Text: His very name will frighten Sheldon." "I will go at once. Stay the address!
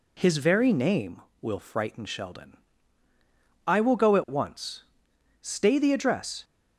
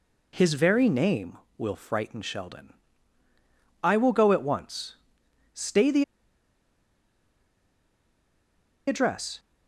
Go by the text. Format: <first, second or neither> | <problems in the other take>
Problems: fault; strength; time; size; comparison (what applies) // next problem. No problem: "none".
first | pauses between "the" and "address"; strong; at 6.0 s; 2.8 s long